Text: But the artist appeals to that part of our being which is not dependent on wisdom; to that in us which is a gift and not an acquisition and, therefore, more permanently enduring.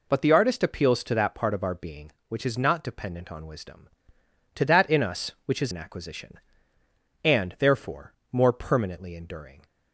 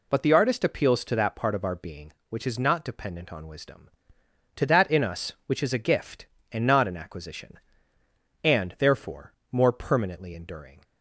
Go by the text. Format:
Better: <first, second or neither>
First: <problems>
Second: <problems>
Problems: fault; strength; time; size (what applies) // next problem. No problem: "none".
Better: second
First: skips "a gift and not"; at 5.7 s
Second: none